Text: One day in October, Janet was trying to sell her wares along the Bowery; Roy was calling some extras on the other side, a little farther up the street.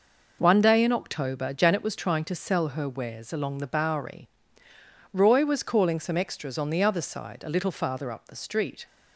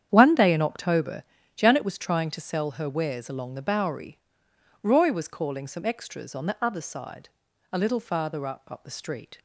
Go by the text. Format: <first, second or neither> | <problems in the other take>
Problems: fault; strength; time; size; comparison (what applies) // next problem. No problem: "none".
first | starts louder than the rest; strong; until 1.1 s; 9 dB // says "up" twice; at 8.6 s